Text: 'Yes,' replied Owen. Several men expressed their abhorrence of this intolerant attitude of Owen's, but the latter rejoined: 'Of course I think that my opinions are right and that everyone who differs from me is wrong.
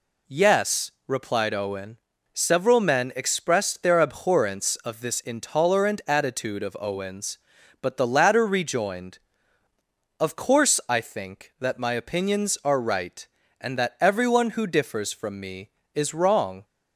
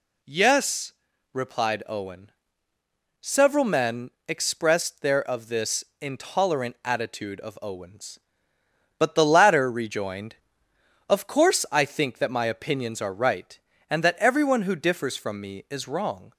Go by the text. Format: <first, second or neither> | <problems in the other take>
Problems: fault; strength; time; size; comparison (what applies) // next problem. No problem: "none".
first | pauses between "men" and "expressed"; slight; at 4.1 s; 0.18 s long // skips "abhorrence"; at 5.2 s // pauses between "this" and "intolerant"; slight; at 5.8 s; 0.18 s long